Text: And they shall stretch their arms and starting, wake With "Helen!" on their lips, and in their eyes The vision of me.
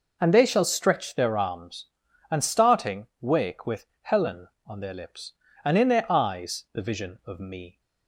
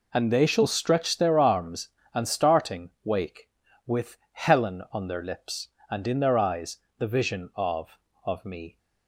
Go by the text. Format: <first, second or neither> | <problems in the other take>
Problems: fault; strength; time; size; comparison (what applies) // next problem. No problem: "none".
first | pauses between "With" and "Helen"; slight; at 4.1 s; 0.16 s long; slight in the first // pauses between "eyes" and "The"; slight; at 6.7 s; 0.20 s long // says "of" twice; at 8.2 s